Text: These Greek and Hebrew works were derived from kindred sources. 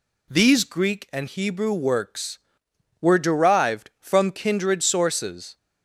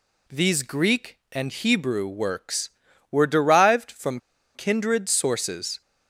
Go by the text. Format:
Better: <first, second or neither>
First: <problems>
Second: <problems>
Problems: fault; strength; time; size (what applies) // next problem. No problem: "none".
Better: first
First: none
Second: pauses between "from" and "kindred"; at 4.1 s; 0.36 s long